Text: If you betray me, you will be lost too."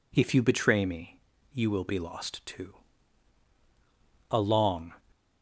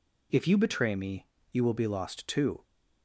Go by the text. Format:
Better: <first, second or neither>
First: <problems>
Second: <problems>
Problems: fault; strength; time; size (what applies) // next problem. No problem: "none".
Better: second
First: goes on to say "A long"; noticeable; from 4.2 s on; 0.64 s long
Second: none